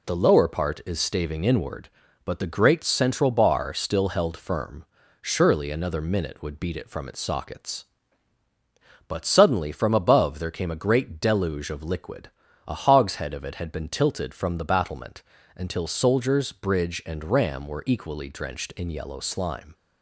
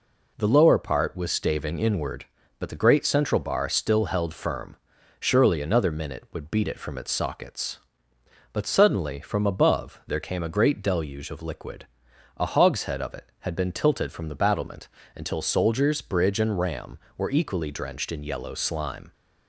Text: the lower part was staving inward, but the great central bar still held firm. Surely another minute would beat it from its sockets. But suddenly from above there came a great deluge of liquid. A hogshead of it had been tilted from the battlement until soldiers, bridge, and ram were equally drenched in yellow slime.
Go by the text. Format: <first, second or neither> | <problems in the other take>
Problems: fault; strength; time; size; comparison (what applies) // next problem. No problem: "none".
second | says "is" for "was"; at 0.8 s // pauses between "battlement" and "until"; slight; at 15.2 s; 0.32 s long; slight in the second